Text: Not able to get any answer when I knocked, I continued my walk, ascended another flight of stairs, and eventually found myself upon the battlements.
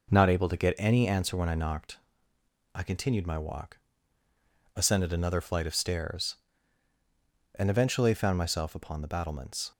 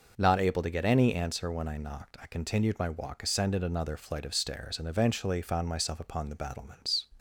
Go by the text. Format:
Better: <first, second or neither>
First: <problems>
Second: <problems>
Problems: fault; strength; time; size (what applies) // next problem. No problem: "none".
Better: neither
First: none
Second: none